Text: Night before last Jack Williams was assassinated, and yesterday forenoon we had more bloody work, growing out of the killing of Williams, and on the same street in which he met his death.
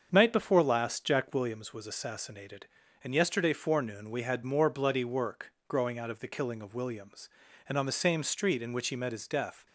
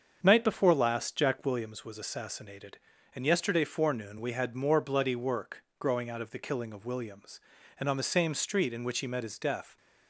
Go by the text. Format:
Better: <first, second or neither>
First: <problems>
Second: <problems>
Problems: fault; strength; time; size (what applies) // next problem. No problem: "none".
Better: neither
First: starts louder than the rest; strong; until 1.1 s; 7 dB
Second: starts louder than the rest; strong; until 1.2 s; 7 dB